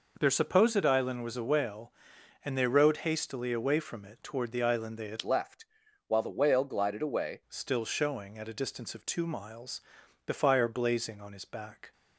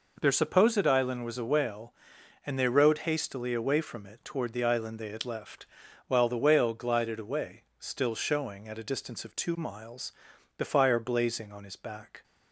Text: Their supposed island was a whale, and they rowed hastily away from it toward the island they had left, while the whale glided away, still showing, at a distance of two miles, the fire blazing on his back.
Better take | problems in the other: second | changes voice from "left" to "away"; from 5.2 to 7.4 s; 2.2 s long

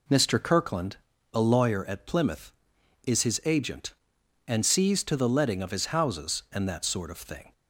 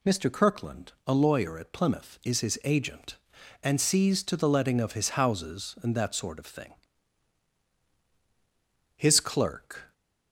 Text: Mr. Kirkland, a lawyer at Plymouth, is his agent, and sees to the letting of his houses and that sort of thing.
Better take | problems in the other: first | goes on to say "His clerk"; noticeable; from 8.9 s on; 0.98 s long

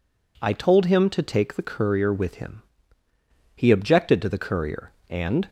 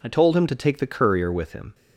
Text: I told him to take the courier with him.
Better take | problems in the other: second | goes on to say "He objected to the courier and"; strong; from 3.5 s on; 1.9 s long

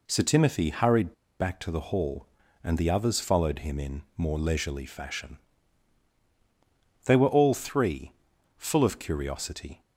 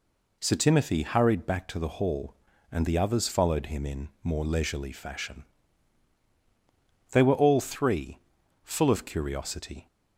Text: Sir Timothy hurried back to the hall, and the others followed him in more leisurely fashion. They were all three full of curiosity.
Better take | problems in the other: second | pauses between "hurried" and "back"; slight; at 1.1 s; 0.26 s long // pauses between "three" and "full"; at 8.1 s; 0.44 s long; also in the second

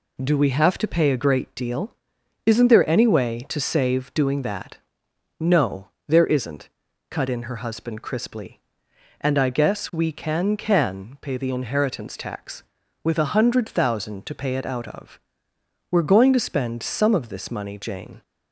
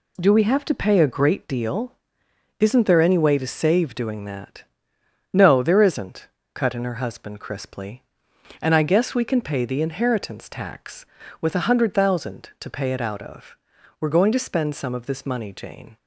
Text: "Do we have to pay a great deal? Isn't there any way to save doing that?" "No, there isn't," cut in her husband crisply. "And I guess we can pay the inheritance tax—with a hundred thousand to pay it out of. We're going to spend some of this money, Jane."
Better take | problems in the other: second | says "can" twice; at 10.5 s

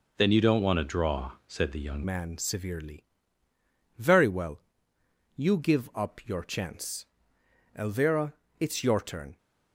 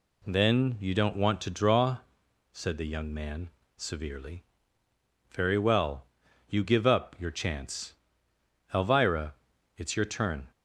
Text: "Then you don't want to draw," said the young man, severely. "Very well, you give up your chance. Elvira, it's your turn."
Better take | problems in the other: second | changes voice at "man"; from 2.0 s on; 7.3 s long

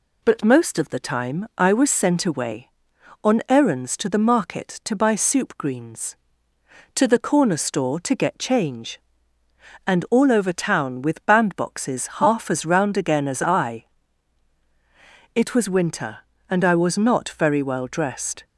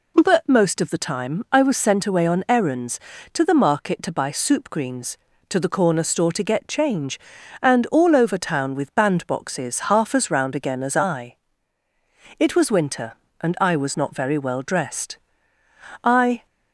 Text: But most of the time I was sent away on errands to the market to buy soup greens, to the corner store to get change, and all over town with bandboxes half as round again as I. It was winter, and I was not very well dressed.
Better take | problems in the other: first | goes on to say "I"; slight; from 16.0 s on; 0.42 s long

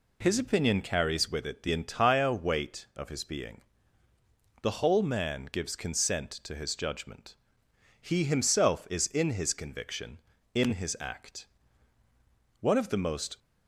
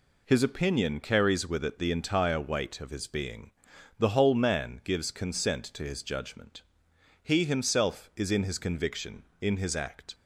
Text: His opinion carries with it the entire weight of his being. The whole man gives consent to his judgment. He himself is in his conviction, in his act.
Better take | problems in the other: second | goes on to say "One of the most"; noticeable; from 12.6 s on; 0.78 s long

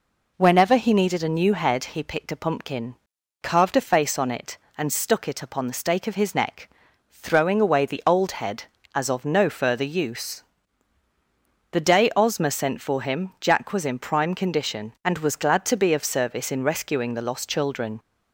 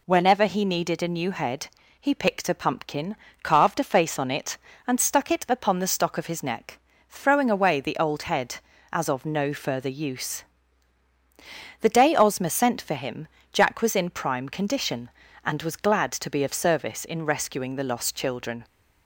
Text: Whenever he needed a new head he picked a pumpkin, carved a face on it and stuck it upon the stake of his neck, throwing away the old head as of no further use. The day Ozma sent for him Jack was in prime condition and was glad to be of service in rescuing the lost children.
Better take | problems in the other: first | pauses between "head" and "he"; slight; at 1.6 s; 0.30 s long // says "stock" for "stake"; at 5.8 s // pauses between "him" and "Jack"; slight; at 13.2 s; 0.24 s long

